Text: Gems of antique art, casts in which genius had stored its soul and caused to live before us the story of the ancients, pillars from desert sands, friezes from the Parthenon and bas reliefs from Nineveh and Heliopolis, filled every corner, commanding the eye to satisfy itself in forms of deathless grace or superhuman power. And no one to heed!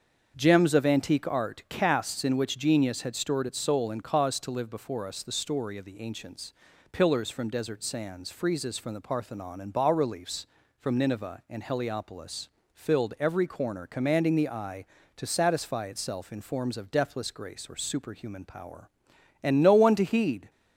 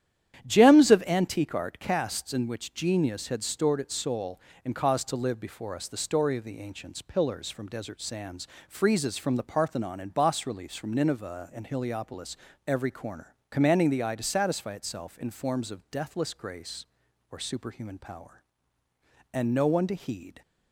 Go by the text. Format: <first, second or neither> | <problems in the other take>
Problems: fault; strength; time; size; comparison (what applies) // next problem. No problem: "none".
first | starts louder than the rest; strong; until 1.5 s; 10 dB; also in the first // skips "filled"; at 12.5 s